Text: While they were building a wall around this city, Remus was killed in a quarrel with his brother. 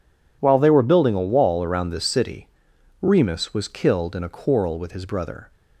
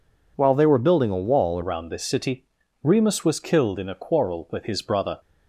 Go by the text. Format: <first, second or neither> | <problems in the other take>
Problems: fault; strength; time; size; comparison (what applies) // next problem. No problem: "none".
first | changes voice at "around"; from 1.6 s on; 3.5 s long